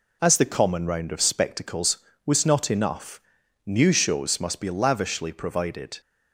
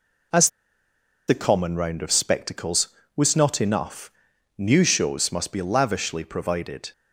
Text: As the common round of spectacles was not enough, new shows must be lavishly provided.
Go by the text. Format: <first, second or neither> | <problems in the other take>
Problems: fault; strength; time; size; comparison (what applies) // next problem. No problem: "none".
first | pauses between "As" and "the"; noticeable; at 0.4 s; 0.78 s long